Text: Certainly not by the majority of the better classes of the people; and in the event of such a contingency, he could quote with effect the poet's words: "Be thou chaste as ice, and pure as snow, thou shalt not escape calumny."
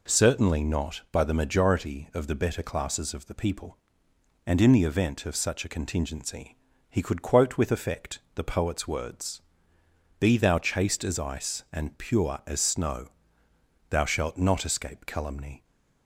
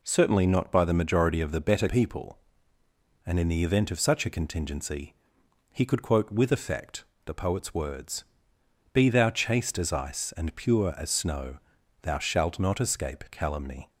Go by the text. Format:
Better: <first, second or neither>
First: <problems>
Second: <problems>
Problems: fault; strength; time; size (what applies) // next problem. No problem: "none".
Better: first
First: pauses between "effect" and "the"; slight; at 8.1 s; 0.16 s long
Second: skips "classes of the"; at 1.8 s // pauses between "effect" and "the"; slight; at 7.0 s; 0.22 s long